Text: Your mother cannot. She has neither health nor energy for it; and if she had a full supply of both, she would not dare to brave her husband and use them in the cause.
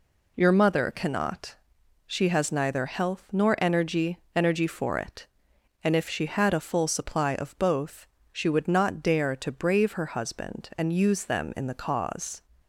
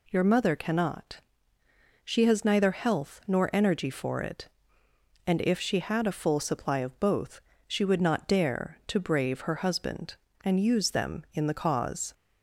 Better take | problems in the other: second | says "energy" twice; at 4.3 s

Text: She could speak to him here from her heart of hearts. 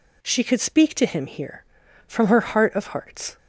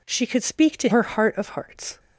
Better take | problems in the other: first | skips "him here from"; at 0.8 s

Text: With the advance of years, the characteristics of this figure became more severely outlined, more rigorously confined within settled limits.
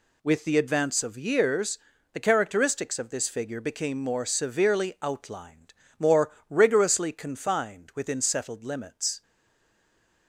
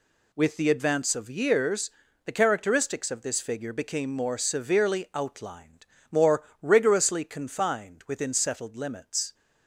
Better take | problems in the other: second | pauses between "more" and "rigorously"; slight; at 6.2 s; 0.20 s long; slight in the second // stays silent after the last word; from 9.2 s on; 1.0 s long

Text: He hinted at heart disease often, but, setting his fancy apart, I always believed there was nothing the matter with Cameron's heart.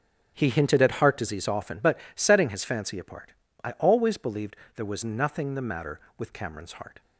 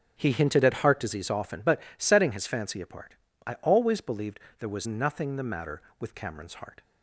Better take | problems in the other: neither | starts louder than the rest; strong; the same in both // pauses between "believed" and "there"; slight; the same in both

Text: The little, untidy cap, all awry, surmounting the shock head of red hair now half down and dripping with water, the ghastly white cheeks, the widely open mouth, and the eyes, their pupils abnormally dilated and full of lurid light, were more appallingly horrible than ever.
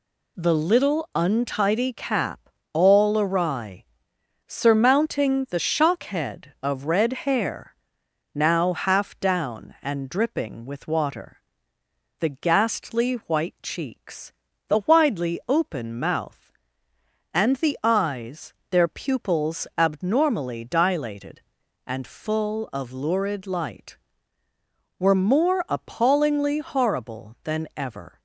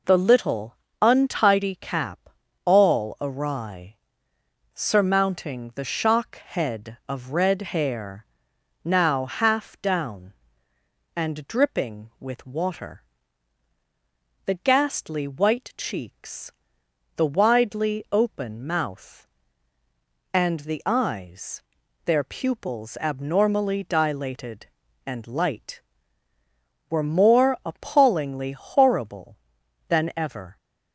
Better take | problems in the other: first | pauses between "hair" and "now"; noticeable; at 8.2 s; 0.58 s long; noticeable in the first // skips "full of lurid"; at 25.2 s

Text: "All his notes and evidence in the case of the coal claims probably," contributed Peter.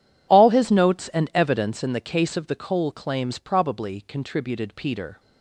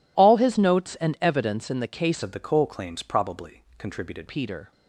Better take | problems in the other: first | changes voice from "of" to "contributed"; from 2.2 to 4.2 s; 2.0 s long

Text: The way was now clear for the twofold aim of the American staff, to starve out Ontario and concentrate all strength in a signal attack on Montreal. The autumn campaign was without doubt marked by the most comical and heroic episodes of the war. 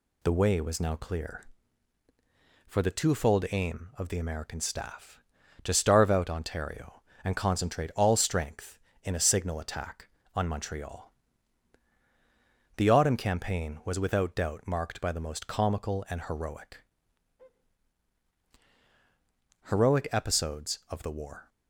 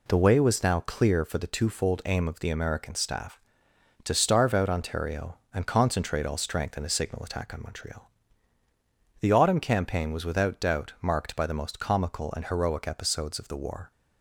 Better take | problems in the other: second | says "heroic" twice; at 19.6 s

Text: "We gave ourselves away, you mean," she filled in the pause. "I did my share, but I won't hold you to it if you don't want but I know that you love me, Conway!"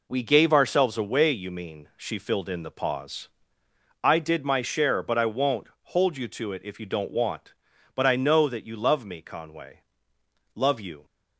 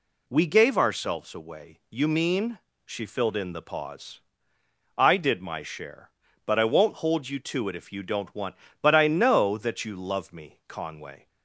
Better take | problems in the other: second | goes on to say "Love you"; from 10.5 s on; 0.50 s long

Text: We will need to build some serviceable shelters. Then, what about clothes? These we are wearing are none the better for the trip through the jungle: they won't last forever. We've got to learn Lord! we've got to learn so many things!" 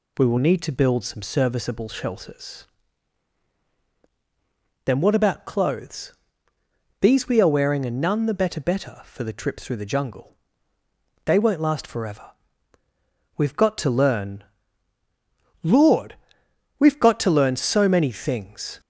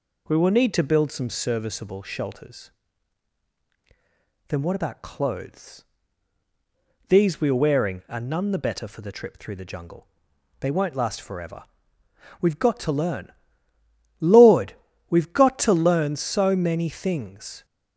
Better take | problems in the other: second | says "better" twice; at 8.6 s // pauses between "learn" and "Lord"; at 14.4 s; 1.2 s long; noticeable in the second

